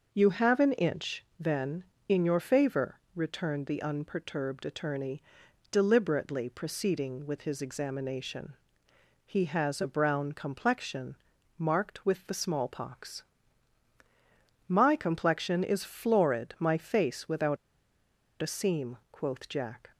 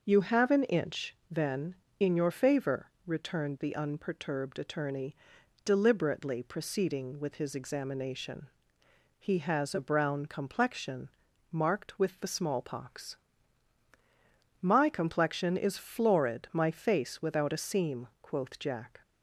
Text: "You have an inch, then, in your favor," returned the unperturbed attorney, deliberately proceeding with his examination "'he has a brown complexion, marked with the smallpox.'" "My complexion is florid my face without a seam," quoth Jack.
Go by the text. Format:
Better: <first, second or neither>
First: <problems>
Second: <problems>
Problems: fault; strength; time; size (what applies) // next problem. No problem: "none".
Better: second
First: starts louder than the rest; until 1.1 s; 6 dB // pauses between "examination" and "he"; noticeable; at 8.5 s; 0.70 s long // pauses between "without" and "a"; noticeable; at 17.5 s; 0.85 s long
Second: starts louder than the rest; until 1.0 s; 6 dB // pauses between "examination" and "he"; noticeable; at 8.4 s; 0.70 s long